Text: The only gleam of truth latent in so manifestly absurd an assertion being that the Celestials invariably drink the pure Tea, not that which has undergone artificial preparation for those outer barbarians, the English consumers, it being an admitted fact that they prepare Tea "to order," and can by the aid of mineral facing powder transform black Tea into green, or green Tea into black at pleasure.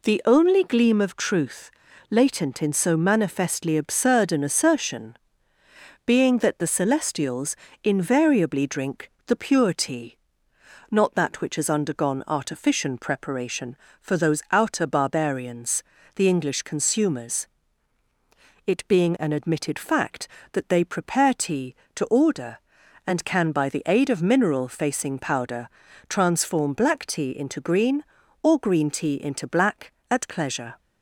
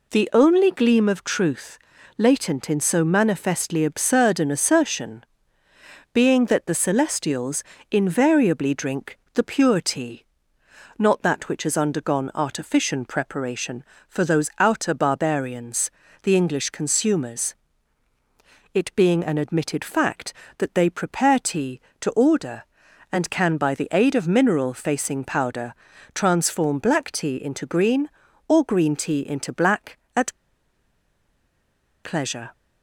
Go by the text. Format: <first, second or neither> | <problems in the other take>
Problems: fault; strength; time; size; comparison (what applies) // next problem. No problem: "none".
first | pauses between "truth" and "latent"; at 1.7 s; 0.40 s long; also in the first // pauses between "assertion" and "being"; noticeable; at 5.2 s; 0.88 s long; noticeable in the first // pauses between "Celestials" and "invariably"; slight; at 7.6 s; 0.26 s long; slight in the first // pauses between "powder" and "transform"; at 25.7 s; 0.40 s long; also in the first // pauses between "at" and "pleasure"; strong; at 30.3 s; 1.7 s long